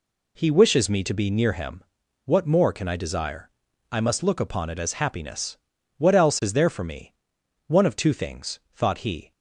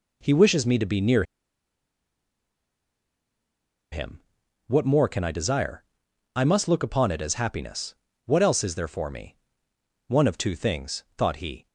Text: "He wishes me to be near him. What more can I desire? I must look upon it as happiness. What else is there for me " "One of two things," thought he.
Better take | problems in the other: first | pauses between "near" and "him"; strong; at 1.2 s; 2.6 s long

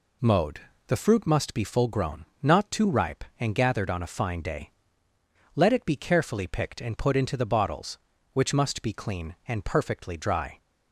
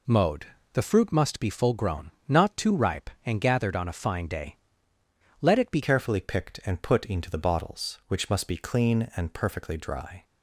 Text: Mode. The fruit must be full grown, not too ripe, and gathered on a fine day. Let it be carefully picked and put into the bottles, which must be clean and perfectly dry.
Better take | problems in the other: first | changes voice at "carefully"; from 5.8 s on; 4.4 s long

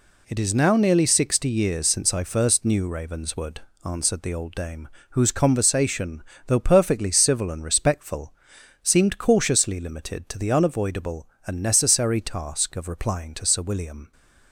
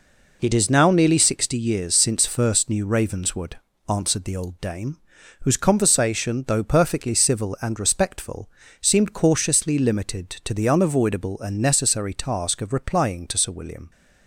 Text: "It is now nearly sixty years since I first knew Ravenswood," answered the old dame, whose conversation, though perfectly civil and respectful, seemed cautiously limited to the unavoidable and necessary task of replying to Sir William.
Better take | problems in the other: first | skips "I"; at 2.2 s

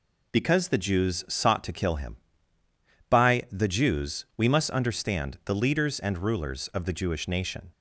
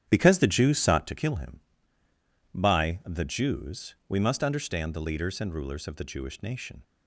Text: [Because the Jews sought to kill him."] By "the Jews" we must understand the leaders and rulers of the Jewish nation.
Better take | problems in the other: first | starts louder than the rest; strong; until 1.1 s; 10 dB

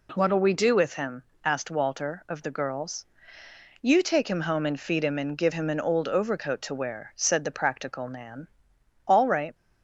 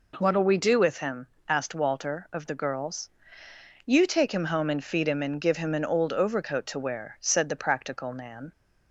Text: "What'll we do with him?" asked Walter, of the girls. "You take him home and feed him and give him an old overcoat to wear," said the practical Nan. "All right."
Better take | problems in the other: first | stops before "All right"; at 8.5 s

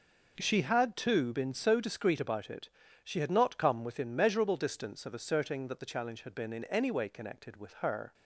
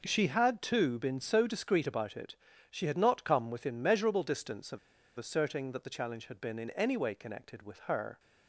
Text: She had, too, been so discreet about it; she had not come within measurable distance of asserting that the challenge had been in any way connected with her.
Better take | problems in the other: first | pauses between "of" and "asserting"; at 4.7 s; 0.38 s long

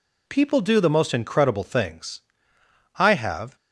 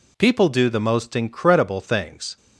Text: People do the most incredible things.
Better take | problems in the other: second | goes on to say "I have"; from 2.9 s on; 0.58 s long

